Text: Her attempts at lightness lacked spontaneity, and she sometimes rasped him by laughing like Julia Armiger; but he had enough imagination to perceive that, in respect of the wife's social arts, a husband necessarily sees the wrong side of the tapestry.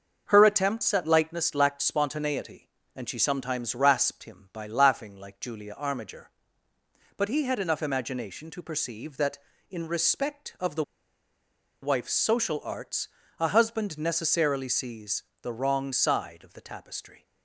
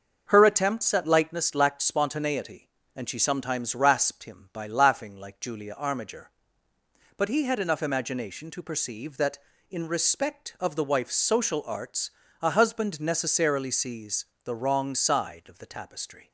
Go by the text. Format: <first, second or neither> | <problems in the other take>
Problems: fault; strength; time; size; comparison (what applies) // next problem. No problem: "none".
second | starts louder than the rest; until 1.2 s; 6.5 dB; also in the second // pauses between "the" and "wife's"; at 10.8 s; 0.98 s long // pauses between "sees" and "the"; slight; at 15.2 s; 0.18 s long; slight in the second